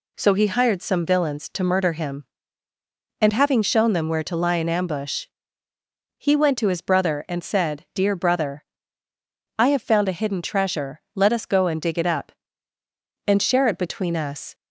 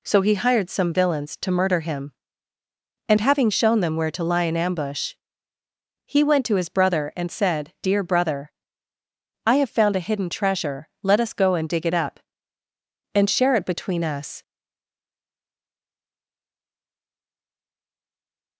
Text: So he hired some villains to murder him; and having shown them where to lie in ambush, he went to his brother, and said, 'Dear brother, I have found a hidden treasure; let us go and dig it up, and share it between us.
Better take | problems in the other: first | stays silent after the last word; strong; from 14.4 s on; 4.1 s long

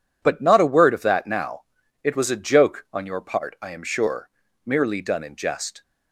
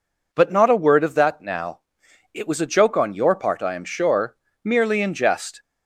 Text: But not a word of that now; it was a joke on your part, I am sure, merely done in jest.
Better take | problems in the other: first | skips "done"; at 5.0 s

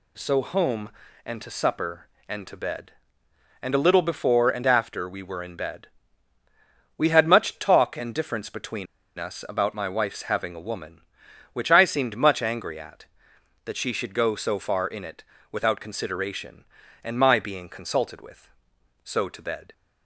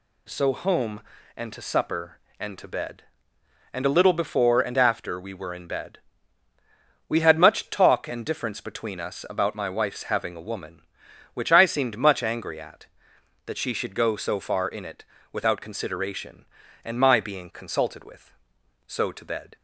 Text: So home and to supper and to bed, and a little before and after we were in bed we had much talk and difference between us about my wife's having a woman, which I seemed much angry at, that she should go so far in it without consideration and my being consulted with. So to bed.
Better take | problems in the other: second | pauses between "bed" and "we"; at 5.8 s; 1.1 s long; also in the second // pauses between "between" and "us"; slight; at 8.8 s; 0.32 s long // pauses between "it" and "without"; slight; at 15.2 s; 0.26 s long; slight in the second

